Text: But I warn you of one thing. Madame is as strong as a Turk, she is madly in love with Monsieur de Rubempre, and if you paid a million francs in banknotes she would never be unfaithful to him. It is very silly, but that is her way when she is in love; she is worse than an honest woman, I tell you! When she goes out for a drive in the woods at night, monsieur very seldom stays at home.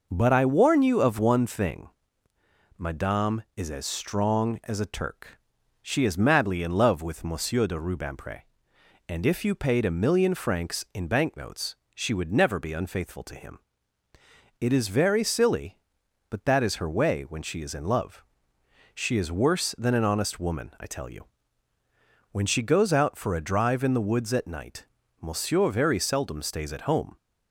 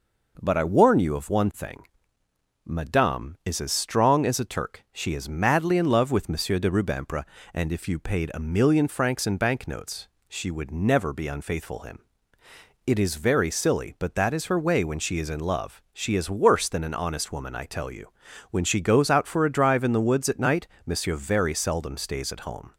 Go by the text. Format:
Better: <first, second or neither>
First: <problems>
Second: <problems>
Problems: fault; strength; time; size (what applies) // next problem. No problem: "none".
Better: first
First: pauses between "banknotes" and "she"; slight; at 11.7 s; 0.18 s long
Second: pauses between "banknotes" and "she"; slight; at 10.0 s; 0.22 s long // skips "to"; at 11.7 s